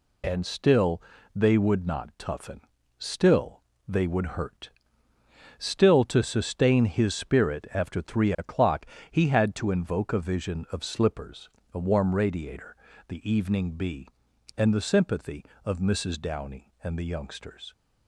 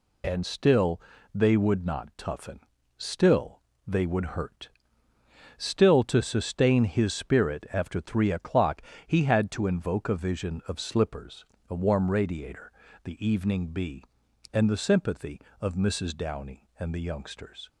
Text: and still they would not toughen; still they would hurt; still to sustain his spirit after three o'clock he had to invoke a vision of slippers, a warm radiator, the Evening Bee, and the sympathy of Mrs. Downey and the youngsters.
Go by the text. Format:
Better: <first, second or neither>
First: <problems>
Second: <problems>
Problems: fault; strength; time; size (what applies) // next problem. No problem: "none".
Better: neither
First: pauses between "still" and "they"; slight; at 1.0 s; 0.34 s long // pauses between "still" and "they"; slight; at 3.6 s; 0.26 s long // pauses between "o'clock" and "he"; slight; at 8.8 s; 0.26 s long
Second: pauses between "still" and "they"; slight; at 0.9 s; 0.34 s long // pauses between "still" and "they"; slight; at 3.5 s; 0.26 s long // pauses between "o'clock" and "he"; slight; at 8.7 s; 0.26 s long